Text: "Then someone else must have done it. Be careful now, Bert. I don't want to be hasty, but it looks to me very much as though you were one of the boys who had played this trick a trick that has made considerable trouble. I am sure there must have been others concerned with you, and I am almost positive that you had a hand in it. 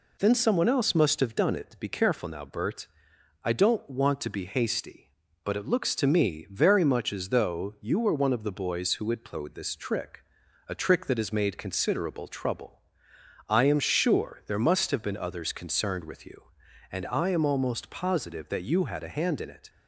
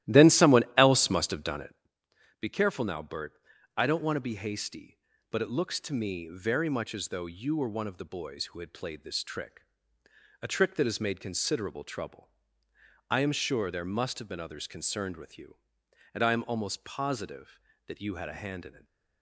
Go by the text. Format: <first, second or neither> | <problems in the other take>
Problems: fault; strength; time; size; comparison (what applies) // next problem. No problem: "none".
first | starts louder than the rest; strong; until 1.9 s; 14.5 dB // pauses between "trick" and "a"; noticeable; at 9.6 s; 0.82 s long; noticeable in the first